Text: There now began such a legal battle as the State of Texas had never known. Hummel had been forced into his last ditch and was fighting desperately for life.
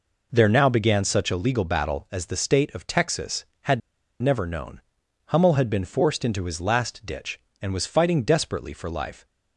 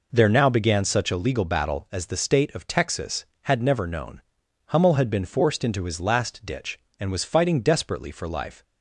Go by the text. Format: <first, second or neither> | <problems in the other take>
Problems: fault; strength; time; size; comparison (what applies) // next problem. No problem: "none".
second | pauses between "had" and "never"; at 3.8 s; 0.42 s long